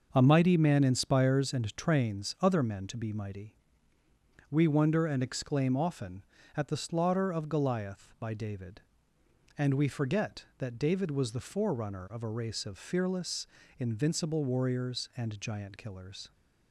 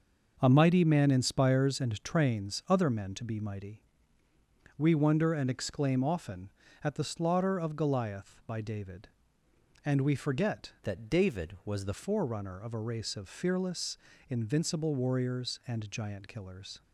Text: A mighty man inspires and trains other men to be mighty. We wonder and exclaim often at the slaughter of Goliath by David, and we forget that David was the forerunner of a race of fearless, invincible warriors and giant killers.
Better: first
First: starts louder than the rest; noticeable; until 1.1 s; 6 dB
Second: starts louder than the rest; noticeable; until 1.4 s; 6 dB // changes voice from "that" to "the"; from 10.8 to 11.9 s; 1.1 s long

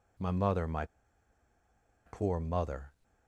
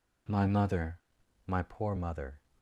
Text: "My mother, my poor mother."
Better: second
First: pauses between "my" and "poor"; at 0.8 s; 1.2 s long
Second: none

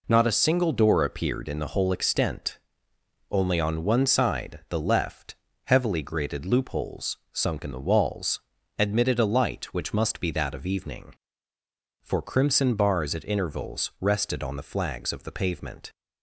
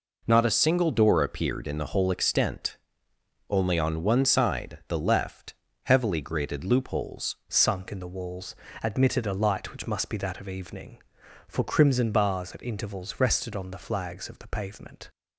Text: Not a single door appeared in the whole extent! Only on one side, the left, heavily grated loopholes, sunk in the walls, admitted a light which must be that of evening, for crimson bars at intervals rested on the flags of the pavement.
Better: first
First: none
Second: changes voice at "sunk"; from 7.4 s on; 7.6 s long

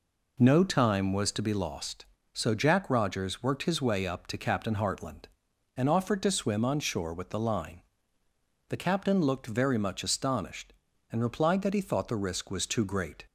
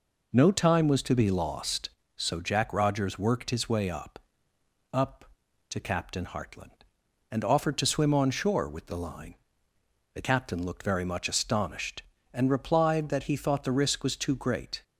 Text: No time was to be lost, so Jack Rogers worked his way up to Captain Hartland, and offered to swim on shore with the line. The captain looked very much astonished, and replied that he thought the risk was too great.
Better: first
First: none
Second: says "up" twice; at 4.9 s

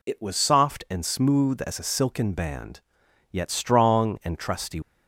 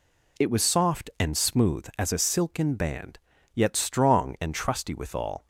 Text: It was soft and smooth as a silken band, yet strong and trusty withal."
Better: second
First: stops before "withal"; at 4.8 s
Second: none

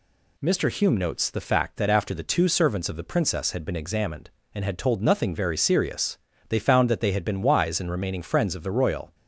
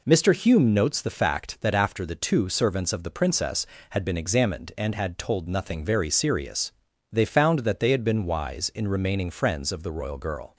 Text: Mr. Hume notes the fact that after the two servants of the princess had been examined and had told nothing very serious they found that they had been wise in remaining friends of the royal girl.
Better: second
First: pauses between "serious" and "they"; slight; at 6.1 s; 0.30 s long // stops before "girl"; at 9.1 s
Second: pauses between "serious" and "they"; at 6.7 s; 0.40 s long

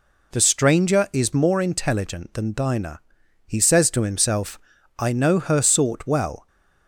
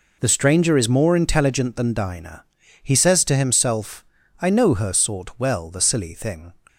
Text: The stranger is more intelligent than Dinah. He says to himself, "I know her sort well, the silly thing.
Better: second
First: stops before "the silly thing"; at 6.4 s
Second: none

